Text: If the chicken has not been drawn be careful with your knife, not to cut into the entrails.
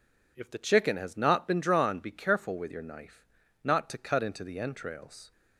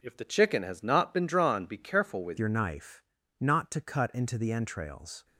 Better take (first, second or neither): first